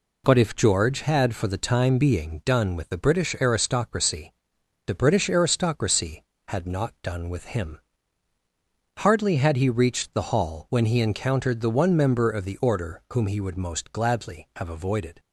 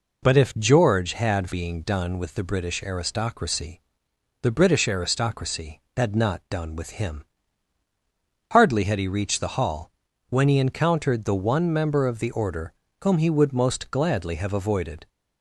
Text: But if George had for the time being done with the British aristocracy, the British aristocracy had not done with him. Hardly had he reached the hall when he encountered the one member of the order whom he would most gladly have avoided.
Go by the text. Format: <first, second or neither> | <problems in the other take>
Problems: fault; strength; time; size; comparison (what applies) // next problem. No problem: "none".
first | skips "for the time"; at 1.5 s // pauses between "hall" and "when"; at 9.8 s; 0.40 s long // pauses between "order" and "whom"; slight; at 12.7 s; 0.30 s long